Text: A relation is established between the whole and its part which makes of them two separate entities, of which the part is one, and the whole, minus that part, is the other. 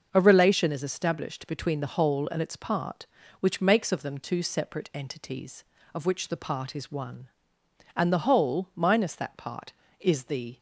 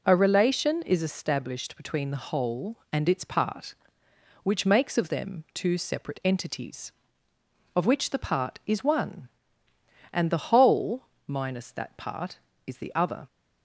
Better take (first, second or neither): second